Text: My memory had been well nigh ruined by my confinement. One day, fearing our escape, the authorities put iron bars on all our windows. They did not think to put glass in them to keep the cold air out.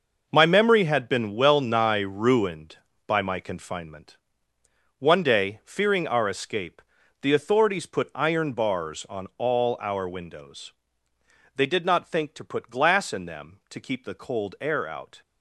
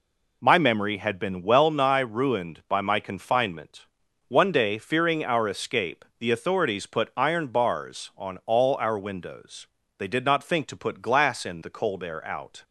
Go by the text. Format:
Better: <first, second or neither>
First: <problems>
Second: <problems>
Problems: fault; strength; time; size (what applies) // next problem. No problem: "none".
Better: first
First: none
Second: skips "them to keep"; at 11.6 s